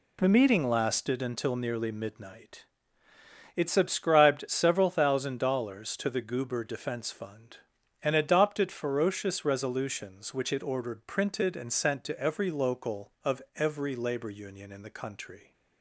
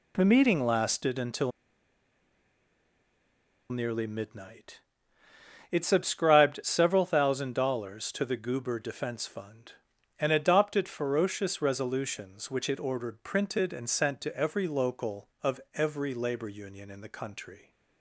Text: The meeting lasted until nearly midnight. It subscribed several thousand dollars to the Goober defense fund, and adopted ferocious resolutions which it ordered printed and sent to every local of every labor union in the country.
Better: first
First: none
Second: pauses between "until" and "nearly"; strong; at 1.5 s; 2.2 s long

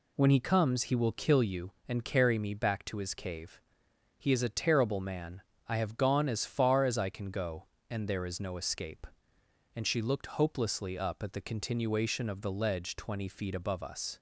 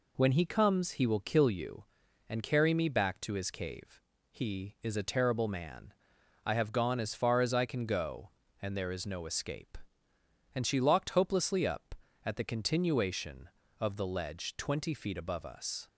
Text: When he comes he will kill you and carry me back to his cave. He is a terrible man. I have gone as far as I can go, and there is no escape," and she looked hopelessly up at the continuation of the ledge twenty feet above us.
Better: first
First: none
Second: says "locked" for "looked"; at 10.7 s

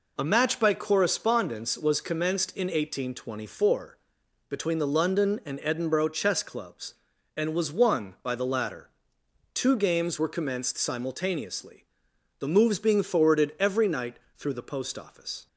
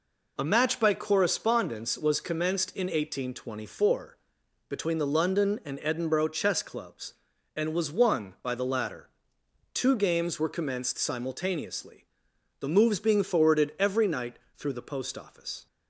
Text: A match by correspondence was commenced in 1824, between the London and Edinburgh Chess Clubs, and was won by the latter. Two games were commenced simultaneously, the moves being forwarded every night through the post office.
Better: neither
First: pauses between "night" and "through"; slight; at 14.1 s; 0.22 s long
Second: pauses between "night" and "through"; slight; at 14.3 s; 0.22 s long

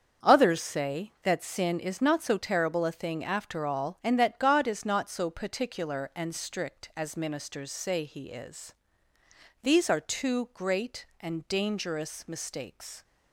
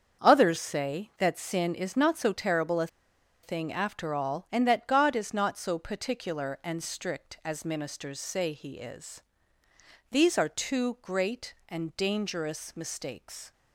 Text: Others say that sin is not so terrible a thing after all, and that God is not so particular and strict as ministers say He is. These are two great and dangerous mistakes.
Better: first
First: starts louder than the rest; strong; until 1.3 s; 7.5 dB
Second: starts louder than the rest; strong; until 1.2 s; 7.5 dB // pauses between "a" and "thing"; noticeable; at 2.8 s; 0.56 s long

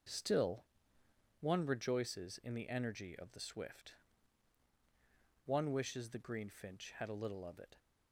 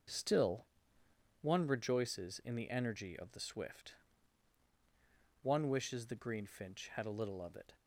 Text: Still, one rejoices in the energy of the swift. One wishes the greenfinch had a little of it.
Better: neither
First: none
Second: none

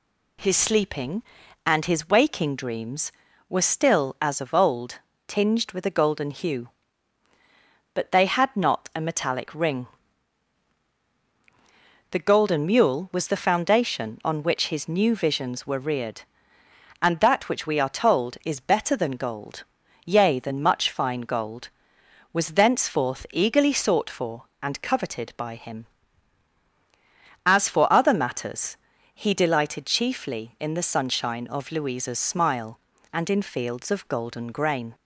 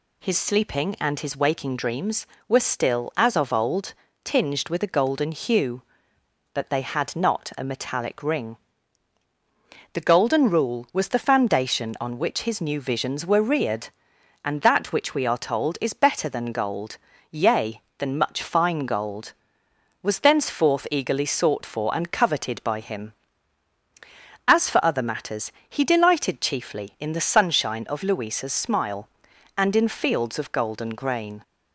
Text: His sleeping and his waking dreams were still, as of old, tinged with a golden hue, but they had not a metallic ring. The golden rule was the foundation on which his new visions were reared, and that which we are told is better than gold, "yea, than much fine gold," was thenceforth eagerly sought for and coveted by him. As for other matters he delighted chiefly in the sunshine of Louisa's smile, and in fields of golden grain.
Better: second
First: says "mule" for "rule"; at 12.6 s // pauses between "matters" and "he"; slight; at 28.7 s; 0.36 s long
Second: pauses between "matters" and "he"; slight; at 25.4 s; 0.20 s long

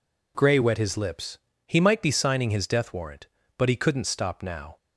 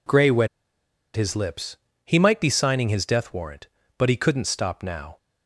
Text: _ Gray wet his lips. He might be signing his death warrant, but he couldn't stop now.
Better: first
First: none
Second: pauses between "wet" and "his"; noticeable; at 0.4 s; 0.67 s long

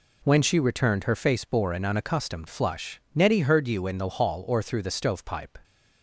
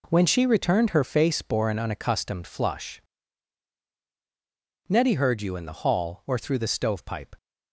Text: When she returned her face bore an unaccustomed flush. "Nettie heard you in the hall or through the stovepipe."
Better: neither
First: none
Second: none

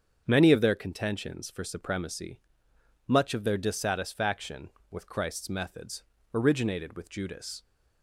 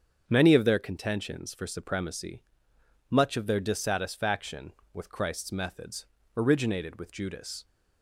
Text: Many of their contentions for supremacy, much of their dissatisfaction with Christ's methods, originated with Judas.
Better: neither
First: starts louder than the rest; strong; until 1.2 s; 7.5 dB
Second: starts louder than the rest; strong; until 1.2 s; 7.5 dB

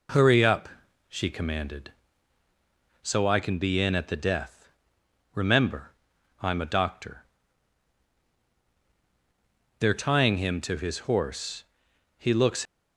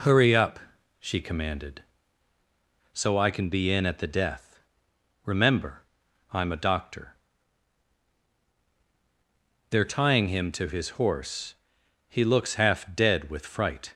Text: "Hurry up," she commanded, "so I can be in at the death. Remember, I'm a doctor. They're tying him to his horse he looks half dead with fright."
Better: second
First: pauses between "horse" and "he"; noticeable; at 11.6 s; 0.56 s long // stops before "half dead with fright"; at 12.6 s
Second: pauses between "horse" and "he"; noticeable; at 11.5 s; 0.56 s long

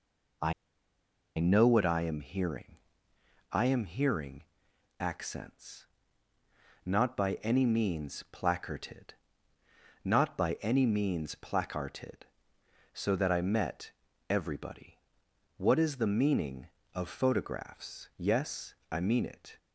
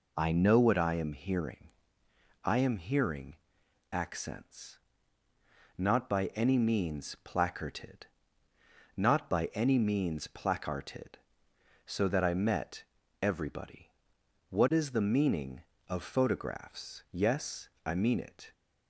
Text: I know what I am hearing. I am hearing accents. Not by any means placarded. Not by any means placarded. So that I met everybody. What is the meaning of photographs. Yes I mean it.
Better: second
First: pauses between "I" and "know"; noticeable; at 0.5 s; 0.84 s long // pauses between "hearing" and "accents"; noticeable; at 4.4 s; 0.56 s long // pauses between "met" and "everybody"; slight; at 13.9 s; 0.36 s long // pauses between "Yes" and "I"; slight; at 18.7 s; 0.16 s long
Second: pauses between "hearing" and "accents"; noticeable; at 3.3 s; 0.56 s long // pauses between "met" and "everybody"; slight; at 12.8 s; 0.36 s long // pauses between "Yes" and "I"; slight; at 17.6 s; 0.16 s long

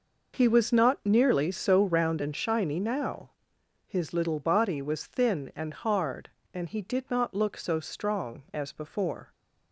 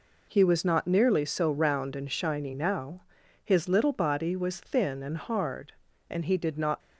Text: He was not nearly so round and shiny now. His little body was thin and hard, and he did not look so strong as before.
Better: first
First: none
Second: stops before "look so strong as before"; at 6.8 s

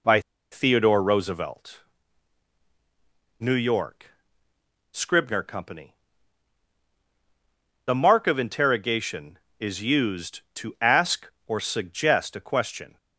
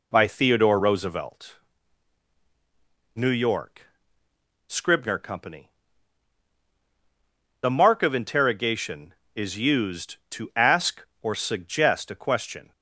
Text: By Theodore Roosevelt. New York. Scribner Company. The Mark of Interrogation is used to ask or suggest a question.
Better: second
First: pauses between "By" and "Theodore"; slight; at 0.1 s; 0.32 s long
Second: none

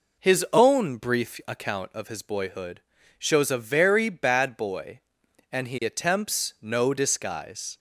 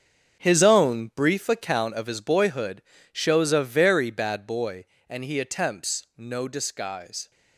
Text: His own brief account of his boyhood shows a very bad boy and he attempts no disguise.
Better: first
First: pauses between "boyhood" and "shows"; at 2.8 s; 0.38 s long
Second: gets quieter; strong; throughout; 12 dB // pauses between "boyhood" and "shows"; slight; at 2.8 s; 0.32 s long

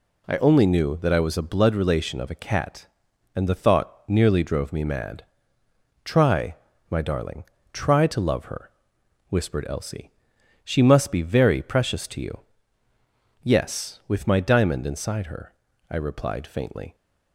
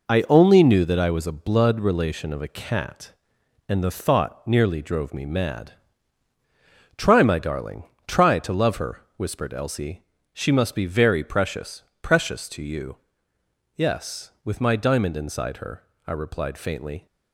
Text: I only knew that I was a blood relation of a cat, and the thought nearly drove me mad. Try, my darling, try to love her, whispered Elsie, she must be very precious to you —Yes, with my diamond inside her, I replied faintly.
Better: first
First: none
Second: says "precious" twice; at 12.0 s

